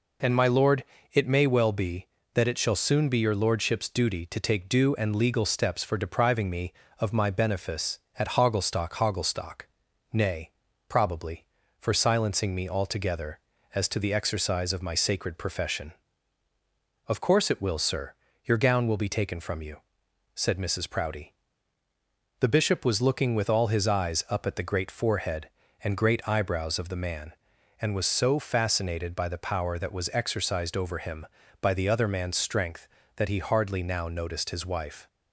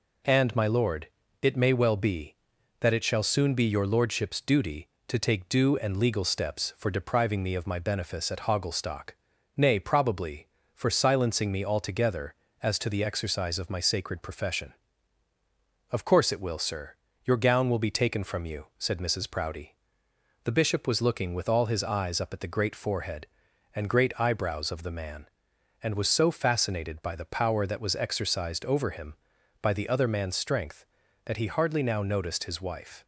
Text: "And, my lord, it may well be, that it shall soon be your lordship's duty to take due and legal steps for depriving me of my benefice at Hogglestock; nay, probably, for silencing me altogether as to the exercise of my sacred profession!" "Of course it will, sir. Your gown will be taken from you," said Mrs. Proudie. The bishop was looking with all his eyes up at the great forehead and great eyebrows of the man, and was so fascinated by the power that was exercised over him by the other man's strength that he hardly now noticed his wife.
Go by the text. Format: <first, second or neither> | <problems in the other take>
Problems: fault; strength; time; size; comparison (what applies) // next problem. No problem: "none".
second | says "Hogglestock" twice; at 8.9 s